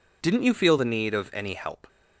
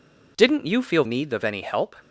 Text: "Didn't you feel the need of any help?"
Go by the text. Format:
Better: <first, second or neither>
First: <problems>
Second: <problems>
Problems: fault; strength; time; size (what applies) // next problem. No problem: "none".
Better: first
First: none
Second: skips "the"; at 1.0 s